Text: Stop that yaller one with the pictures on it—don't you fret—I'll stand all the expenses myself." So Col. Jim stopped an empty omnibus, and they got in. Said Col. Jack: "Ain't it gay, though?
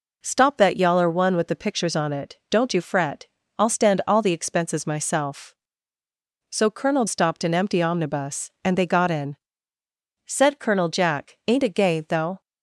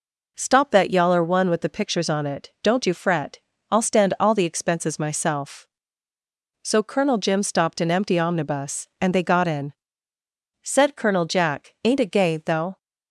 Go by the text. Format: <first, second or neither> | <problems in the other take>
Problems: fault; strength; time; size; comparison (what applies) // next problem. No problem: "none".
second | skips "Jim"; at 7.0 s